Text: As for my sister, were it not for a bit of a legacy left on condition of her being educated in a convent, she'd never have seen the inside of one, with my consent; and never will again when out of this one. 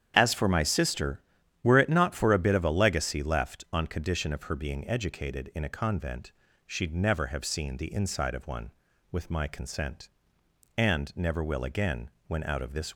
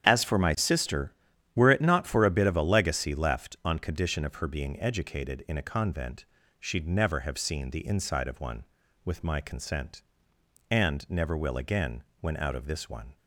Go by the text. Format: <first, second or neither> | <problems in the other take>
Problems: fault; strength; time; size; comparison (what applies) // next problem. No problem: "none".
second | starts louder than the rest; strong; until 1.1 s; 9 dB; strong in the second // pauses between "again" and "when"; slight; at 12.0 s; 0.18 s long; slight in the second // stops before "one"; at 12.9 s